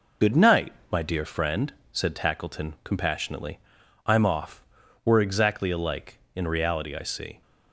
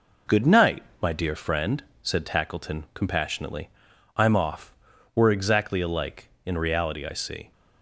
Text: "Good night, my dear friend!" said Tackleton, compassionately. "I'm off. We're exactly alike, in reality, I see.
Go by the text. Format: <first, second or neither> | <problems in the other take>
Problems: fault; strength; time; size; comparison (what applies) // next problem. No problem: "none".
second | loses the start of "Good"; at 0.2 s; 40 ms